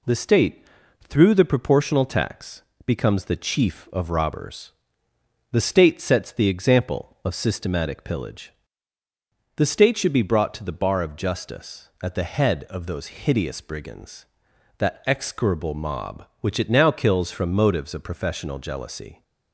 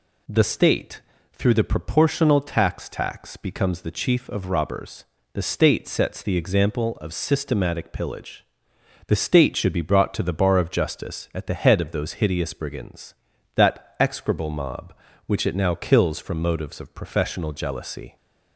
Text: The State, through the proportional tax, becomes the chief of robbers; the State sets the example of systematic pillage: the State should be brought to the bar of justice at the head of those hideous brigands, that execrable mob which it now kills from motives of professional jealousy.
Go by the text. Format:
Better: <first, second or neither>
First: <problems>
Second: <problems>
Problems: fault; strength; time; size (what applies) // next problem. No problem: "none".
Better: first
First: none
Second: says "tax" twice; at 2.8 s